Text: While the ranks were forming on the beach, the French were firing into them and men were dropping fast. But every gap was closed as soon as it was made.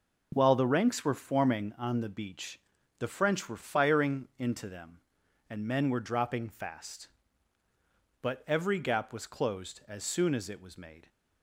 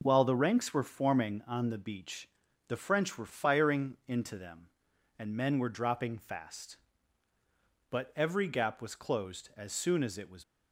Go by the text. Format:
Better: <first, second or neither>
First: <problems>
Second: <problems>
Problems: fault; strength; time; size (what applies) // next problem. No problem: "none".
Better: first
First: none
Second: stops before "made"; at 10.4 s